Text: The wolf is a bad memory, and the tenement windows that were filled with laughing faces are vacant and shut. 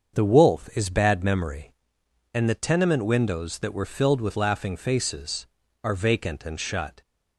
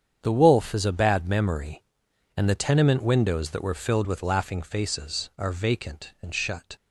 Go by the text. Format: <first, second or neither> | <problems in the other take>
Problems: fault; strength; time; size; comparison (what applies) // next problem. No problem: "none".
second | starts louder than the rest; until 1.2 s; 6.5 dB; strong in the second // skips "a"; at 0.9 s